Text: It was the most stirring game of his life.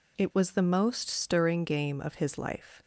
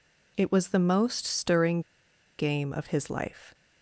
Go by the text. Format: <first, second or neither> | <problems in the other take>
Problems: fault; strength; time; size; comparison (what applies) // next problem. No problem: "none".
first | pauses between "stirring" and "game"; noticeable; at 1.8 s; 0.58 s long